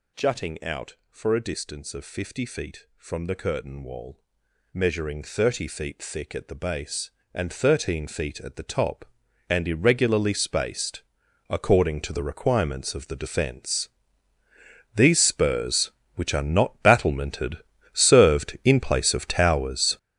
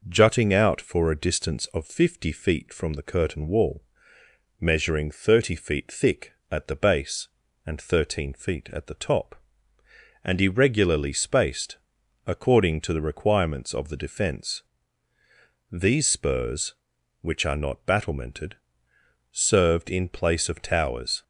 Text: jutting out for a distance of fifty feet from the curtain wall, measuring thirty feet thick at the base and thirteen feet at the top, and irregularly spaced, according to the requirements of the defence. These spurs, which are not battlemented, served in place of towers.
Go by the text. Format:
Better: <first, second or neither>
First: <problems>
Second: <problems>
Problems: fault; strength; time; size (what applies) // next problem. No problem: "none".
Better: second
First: gets louder; strong; throughout; 11.5 dB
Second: none